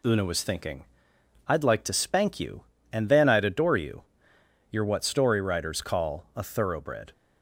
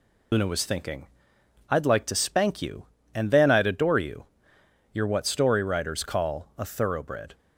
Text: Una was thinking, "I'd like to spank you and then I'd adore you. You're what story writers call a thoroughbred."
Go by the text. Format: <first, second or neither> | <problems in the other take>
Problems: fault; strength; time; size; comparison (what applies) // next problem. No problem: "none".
first | loses the start of "Una"; at 0.3 s; 60 ms